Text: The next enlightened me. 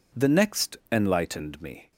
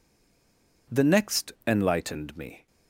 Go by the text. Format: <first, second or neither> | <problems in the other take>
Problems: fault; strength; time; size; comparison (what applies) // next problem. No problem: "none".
first | stays silent before the first word; slight; until 0.8 s; 0.8 s long // pauses between "next" and "enlightened"; slight; at 1.5 s; 0.16 s long; slight in the first